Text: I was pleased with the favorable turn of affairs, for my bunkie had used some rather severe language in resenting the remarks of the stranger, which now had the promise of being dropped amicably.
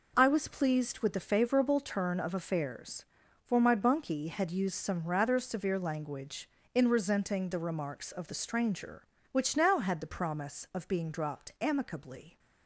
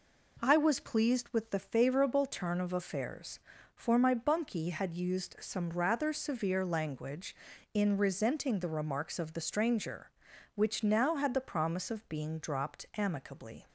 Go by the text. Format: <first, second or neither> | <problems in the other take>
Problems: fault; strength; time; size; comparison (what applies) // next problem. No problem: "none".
neither | none